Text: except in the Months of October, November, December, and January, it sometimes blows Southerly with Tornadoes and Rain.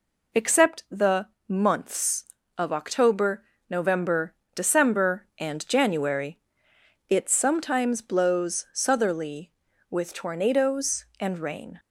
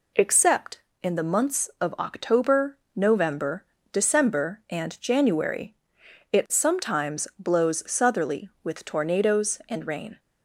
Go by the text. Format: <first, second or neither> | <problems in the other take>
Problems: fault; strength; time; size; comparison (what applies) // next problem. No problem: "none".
second | skips "in"; at 0.8 s // pauses between "the" and "Months"; slight; at 1.2 s; 0.22 s long